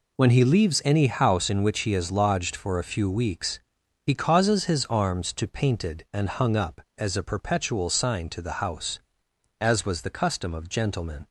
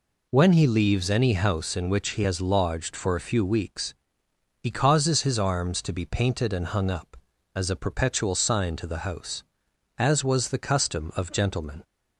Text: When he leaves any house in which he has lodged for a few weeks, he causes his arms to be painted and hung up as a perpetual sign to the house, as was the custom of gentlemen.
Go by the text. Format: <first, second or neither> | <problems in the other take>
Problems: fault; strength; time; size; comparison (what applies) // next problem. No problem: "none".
second | skips "be"; at 5.4 s